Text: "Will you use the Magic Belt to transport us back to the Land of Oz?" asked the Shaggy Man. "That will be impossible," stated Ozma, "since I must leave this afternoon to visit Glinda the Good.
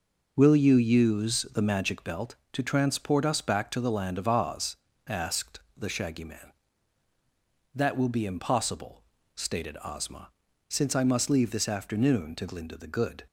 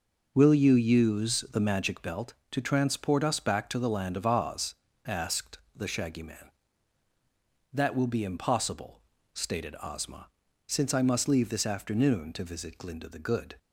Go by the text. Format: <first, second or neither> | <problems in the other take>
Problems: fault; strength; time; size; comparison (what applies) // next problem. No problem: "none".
second | pauses between "asked" and "the"; slight; at 5.5 s; 0.16 s long; slight in the second // skips "visit"; at 12.4 s